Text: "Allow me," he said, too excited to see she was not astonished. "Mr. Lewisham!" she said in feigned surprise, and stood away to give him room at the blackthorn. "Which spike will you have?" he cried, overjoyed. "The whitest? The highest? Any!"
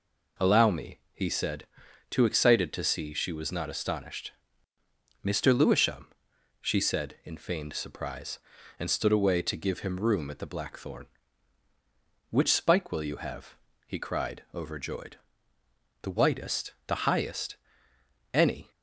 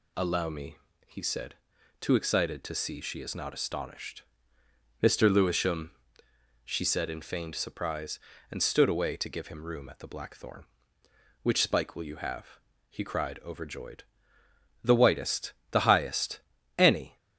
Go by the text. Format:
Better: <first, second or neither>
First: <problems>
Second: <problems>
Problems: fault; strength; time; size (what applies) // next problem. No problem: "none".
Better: first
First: none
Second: says "is" for "was"; at 3.2 s